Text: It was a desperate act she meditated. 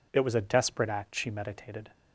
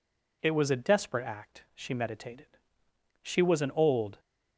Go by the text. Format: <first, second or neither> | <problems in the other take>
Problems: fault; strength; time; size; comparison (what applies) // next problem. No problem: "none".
first | goes on to say "She was an old"; noticeable; from 3.2 s on; 0.98 s long